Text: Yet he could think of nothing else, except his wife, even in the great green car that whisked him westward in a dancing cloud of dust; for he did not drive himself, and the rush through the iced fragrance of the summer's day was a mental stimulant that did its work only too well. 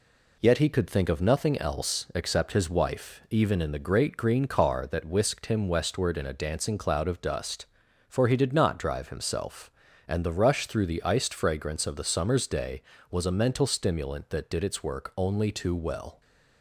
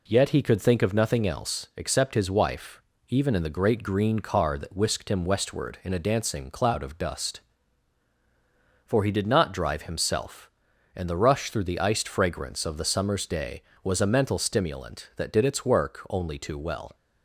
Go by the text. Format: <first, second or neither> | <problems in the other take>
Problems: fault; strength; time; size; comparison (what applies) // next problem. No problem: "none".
neither | none